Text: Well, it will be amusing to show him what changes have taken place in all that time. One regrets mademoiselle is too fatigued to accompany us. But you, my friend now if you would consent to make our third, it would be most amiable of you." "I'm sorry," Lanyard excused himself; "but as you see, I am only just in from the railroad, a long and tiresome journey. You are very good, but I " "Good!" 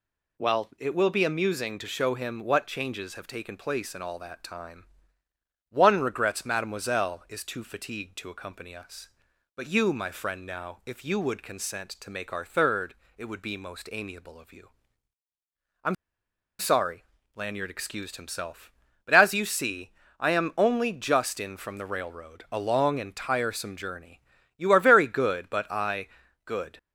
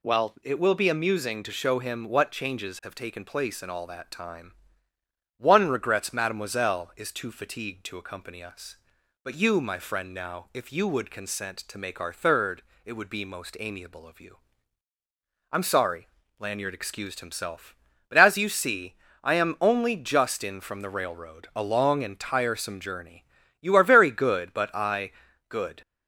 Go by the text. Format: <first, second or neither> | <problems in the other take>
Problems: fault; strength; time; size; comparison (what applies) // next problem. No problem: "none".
second | pauses between "I'm" and "sorry"; noticeable; at 15.9 s; 0.64 s long